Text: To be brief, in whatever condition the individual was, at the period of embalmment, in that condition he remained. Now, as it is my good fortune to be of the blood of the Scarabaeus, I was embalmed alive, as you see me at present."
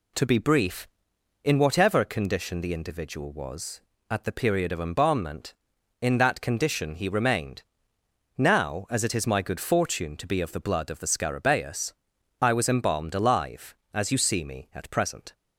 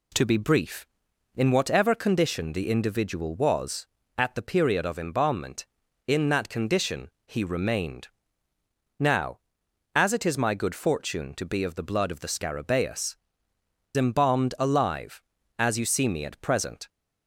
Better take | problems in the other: first | pauses between "condition" and "he"; slight; at 7.0 s; 0.16 s long // skips "I was"; at 13.5 s

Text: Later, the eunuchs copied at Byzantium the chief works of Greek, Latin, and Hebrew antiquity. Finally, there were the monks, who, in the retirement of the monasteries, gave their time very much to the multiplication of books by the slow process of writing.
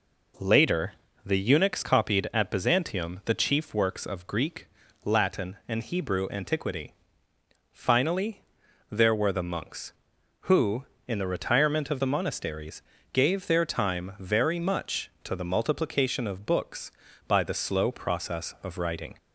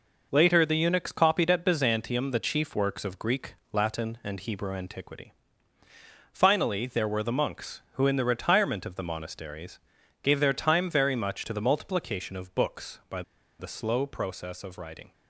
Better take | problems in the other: first | pauses between "by" and "the"; at 13.2 s; 0.37 s long

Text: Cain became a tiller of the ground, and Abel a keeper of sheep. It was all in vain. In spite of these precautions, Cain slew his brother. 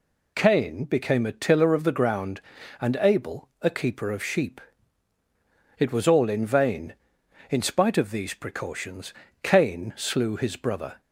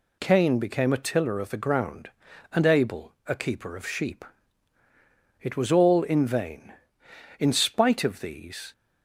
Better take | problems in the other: first | stops before "precautions Cain slew his brother"; at 8.7 s

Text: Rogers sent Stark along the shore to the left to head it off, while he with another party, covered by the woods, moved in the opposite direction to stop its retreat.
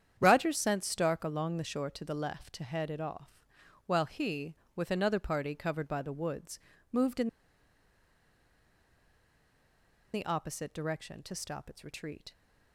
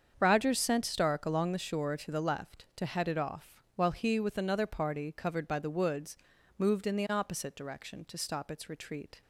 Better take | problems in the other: second | starts louder than the rest; strong; until 1.2 s; 9 dB; strong in the second // pauses between "in" and "the"; strong; at 7.2 s; 2.8 s long

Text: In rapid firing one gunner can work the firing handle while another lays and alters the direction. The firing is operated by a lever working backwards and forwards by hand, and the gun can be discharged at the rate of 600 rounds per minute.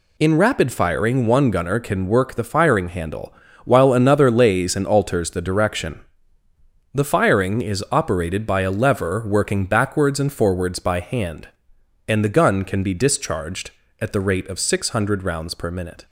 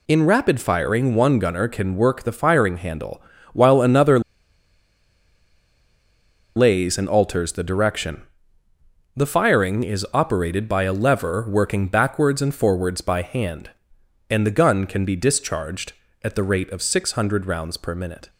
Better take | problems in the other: first | pauses between "handle" and "while"; slight; at 3.2 s; 0.30 s long; slight in the first // pauses between "another" and "lays"; strong; at 4.1 s; 2.3 s long

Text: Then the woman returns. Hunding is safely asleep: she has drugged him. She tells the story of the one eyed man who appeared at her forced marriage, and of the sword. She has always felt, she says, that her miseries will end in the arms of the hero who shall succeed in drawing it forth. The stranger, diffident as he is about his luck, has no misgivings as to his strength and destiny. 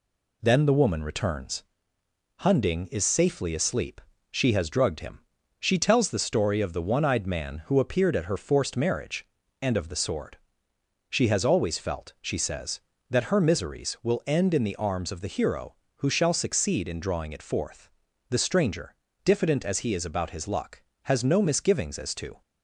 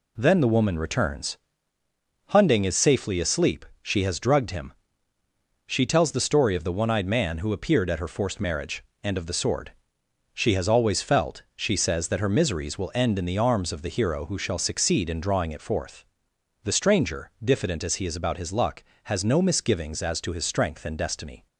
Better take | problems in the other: second | stops before "his strength and destiny"; at 22.4 s

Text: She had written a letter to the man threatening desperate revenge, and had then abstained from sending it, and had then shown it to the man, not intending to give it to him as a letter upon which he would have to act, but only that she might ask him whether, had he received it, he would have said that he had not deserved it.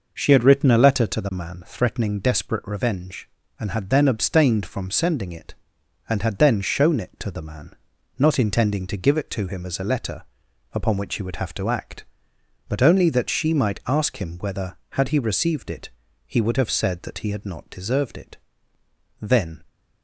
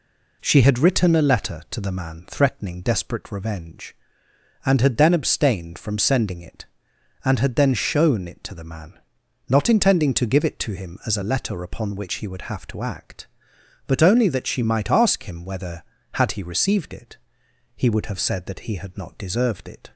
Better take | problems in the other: second | pauses between "letter" and "upon"; noticeable; at 10.2 s; 0.48 s long // goes on to say "Then"; slight; from 19.2 s on; 0.42 s long

